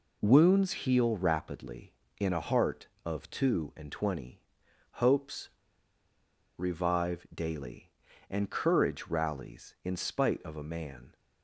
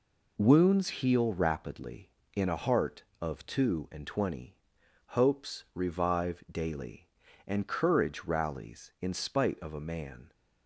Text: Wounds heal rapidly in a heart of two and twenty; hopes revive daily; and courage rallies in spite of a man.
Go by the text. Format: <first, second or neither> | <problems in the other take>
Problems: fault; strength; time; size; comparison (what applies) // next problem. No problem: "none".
second | pauses between "hopes" and "revive"; at 5.4 s; 1.0 s long